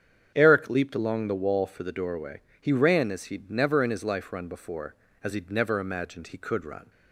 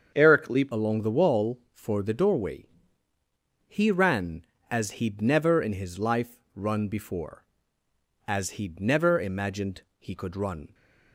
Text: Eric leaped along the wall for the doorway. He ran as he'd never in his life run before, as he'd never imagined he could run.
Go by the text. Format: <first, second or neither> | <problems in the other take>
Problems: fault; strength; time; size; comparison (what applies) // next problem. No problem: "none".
first | starts louder than the rest; strong; until 1.1 s; 7 dB; strong in the first // changes voice at "along"; from 0.7 s on; 10.0 s long // pauses between "imagined" and "he"; slight; at 9.8 s; 0.16 s long